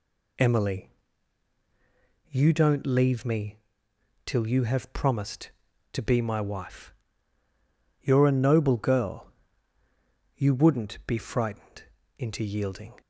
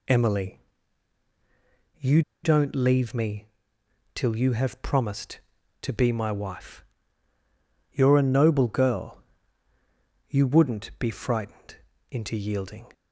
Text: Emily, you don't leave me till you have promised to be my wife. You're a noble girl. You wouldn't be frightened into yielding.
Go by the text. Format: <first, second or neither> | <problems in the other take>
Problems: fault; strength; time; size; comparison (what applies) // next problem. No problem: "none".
first | pauses between "you" and "don't"; slight; at 2.2 s; 0.22 s long // pauses between "me" and "till"; noticeable; at 3.4 s; 0.66 s long; noticeable in the first // pauses between "frightened" and "into"; slight; at 11.7 s; 0.34 s long; slight in the first